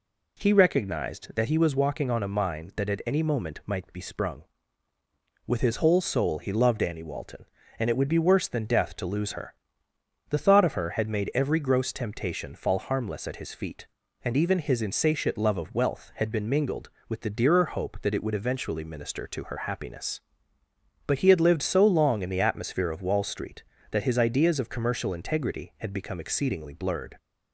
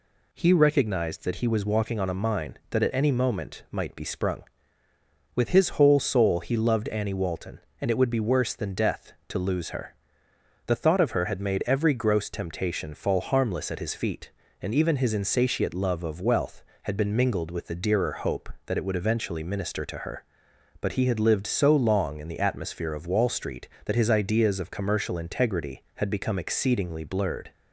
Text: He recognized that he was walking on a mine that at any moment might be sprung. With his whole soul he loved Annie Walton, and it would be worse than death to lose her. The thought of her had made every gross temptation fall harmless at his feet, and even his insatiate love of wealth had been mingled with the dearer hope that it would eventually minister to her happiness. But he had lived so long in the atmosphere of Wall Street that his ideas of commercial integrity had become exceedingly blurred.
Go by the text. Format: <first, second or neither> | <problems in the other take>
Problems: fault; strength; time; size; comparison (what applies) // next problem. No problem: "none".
first | skips "happiness"; at 20.5 s